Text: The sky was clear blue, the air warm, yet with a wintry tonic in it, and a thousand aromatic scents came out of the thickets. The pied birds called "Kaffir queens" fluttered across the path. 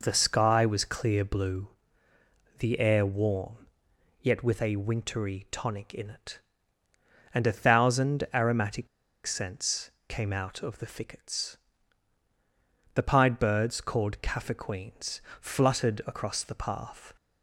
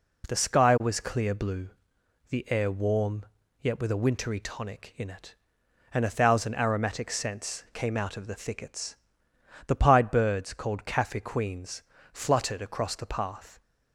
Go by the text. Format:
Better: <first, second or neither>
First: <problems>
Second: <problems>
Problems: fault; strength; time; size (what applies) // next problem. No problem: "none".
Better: second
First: pauses between "aromatic" and "scents"; at 8.8 s; 0.39 s long // pauses between "scents" and "came"; slight; at 9.9 s; 0.16 s long // pauses between "queens" and "fluttered"; slight; at 15.2 s; 0.20 s long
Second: pauses between "queens" and "fluttered"; slight; at 11.8 s; 0.30 s long